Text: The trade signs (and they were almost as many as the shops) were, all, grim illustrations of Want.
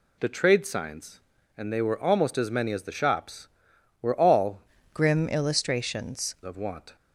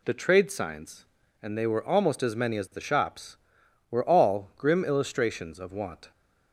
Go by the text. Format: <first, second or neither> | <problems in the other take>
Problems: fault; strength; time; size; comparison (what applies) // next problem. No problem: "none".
second | changes voice from "grim" to "illustrations"; from 4.9 to 6.3 s; 1.4 s long